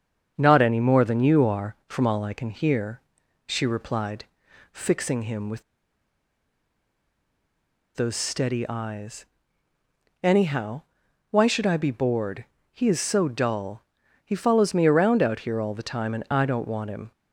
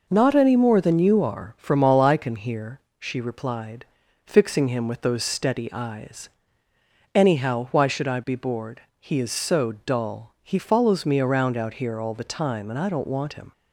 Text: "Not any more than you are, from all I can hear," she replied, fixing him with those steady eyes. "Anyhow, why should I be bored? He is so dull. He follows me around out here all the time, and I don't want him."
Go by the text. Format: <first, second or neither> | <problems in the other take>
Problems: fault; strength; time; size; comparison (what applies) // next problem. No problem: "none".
second | starts louder than the rest; until 1.3 s; 7 dB // pauses between "with" and "those"; strong; at 5.6 s; 2.3 s long